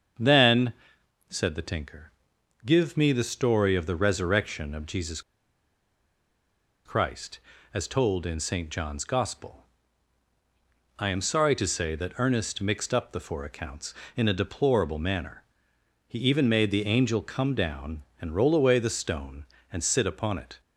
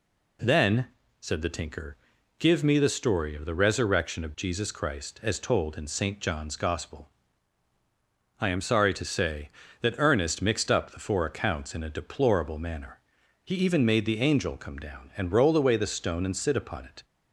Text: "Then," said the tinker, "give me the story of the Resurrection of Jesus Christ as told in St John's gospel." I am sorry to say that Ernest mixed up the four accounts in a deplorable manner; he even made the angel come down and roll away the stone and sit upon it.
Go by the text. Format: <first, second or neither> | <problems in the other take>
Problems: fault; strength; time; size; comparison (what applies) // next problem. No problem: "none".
second | starts louder than the rest; until 1.7 s; 7 dB // pauses between "Jesus" and "Christ"; strong; at 5.1 s; 1.6 s long